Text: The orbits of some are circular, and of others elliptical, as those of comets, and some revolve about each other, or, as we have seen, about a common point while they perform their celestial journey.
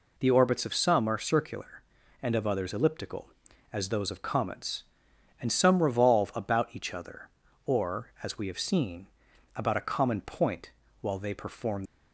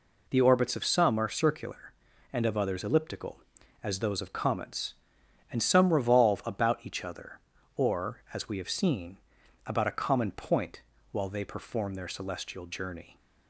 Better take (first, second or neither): second